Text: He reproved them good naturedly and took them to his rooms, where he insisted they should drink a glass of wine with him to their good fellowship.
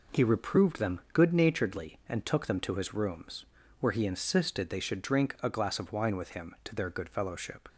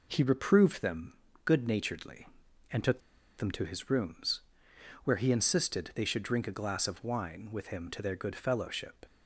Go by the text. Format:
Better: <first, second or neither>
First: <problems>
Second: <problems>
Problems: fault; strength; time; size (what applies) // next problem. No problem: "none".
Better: first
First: none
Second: pauses between "them" and "good"; slight; at 1.1 s; 0.32 s long // pauses between "took" and "them"; at 2.9 s; 0.38 s long